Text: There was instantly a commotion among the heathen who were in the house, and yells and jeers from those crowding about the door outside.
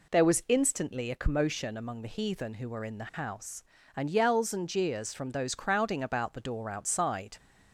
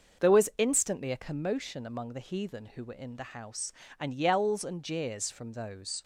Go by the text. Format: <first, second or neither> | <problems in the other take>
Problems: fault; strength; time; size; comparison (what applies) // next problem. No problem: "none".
first | stops before "crowding about the door outside"; at 6.0 s